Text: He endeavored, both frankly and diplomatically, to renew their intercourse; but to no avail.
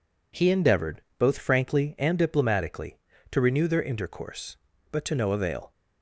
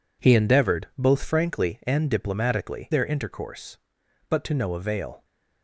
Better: first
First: none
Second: skips "to renew"; at 2.9 s

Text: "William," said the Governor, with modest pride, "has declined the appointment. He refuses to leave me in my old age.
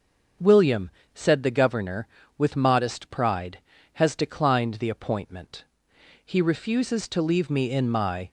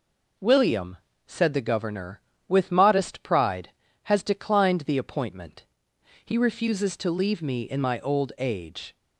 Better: second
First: starts louder than the rest; until 1.6 s; 6.5 dB // stops before "old age"; at 8.2 s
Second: none

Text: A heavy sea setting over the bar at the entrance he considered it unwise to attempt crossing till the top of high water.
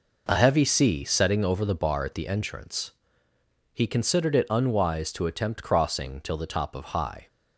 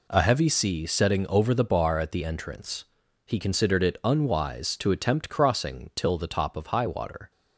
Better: second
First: pauses between "entrance" and "he"; noticeable; at 2.9 s; 0.82 s long // stops before "water"; at 7.2 s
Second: pauses between "entrance" and "he"; at 2.8 s; 0.44 s long

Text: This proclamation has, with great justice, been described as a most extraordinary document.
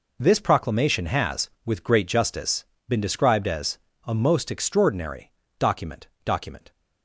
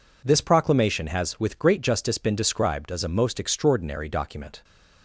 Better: second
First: pauses between "as" and "a"; slight; at 3.7 s; 0.28 s long // pauses between "extraordinary" and "document"; slight; at 5.3 s; 0.28 s long // says "document" twice; at 6.2 s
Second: none

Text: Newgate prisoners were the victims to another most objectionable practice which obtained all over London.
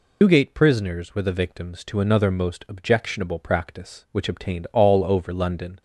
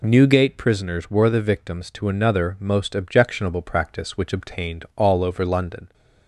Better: second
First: loses the start of "Newgate"; at 0.2 s; 120 ms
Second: none

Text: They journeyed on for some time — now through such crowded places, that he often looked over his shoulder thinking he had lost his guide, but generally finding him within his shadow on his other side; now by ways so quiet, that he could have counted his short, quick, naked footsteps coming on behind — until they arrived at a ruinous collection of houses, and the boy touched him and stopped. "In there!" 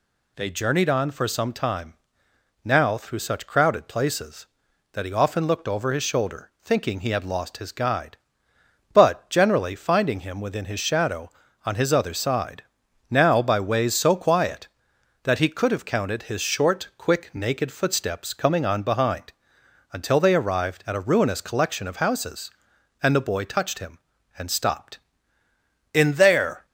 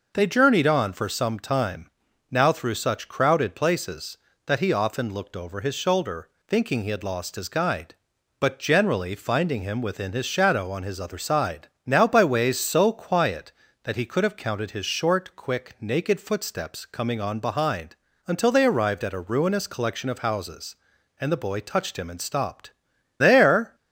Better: first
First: none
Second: pauses between "shoulder" and "thinking"; slight; at 6.2 s; 0.20 s long // skips "In"; at 22.9 s

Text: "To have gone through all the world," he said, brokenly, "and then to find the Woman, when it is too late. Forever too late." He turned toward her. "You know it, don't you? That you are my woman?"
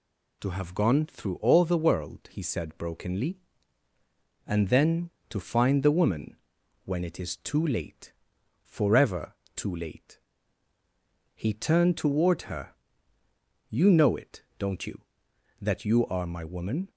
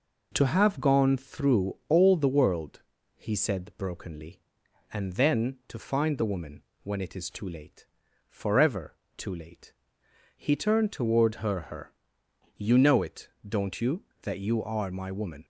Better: first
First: pauses between "Forever" and "too"; slight; at 9.3 s; 0.22 s long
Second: pauses between "Forever" and "too"; slight; at 8.9 s; 0.24 s long // says "her" twice; at 11.6 s

